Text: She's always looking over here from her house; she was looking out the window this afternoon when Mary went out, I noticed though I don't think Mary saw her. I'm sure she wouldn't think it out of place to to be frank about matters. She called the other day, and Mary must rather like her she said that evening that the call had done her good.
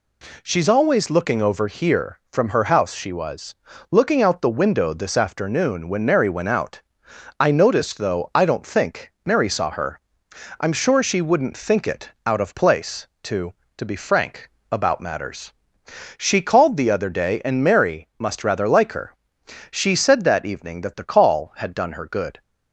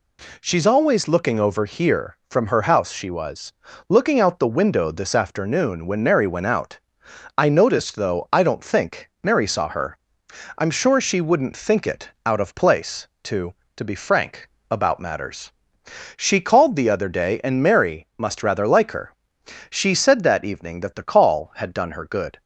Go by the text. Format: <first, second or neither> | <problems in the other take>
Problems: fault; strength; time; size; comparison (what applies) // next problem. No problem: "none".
neither | pauses between "was" and "looking"; slight; the same in both // pauses between "it" and "out"; slight; the same in both // pauses between "frank" and "about"; slight; the same in both // pauses between "her" and "she"; noticeable; the same in both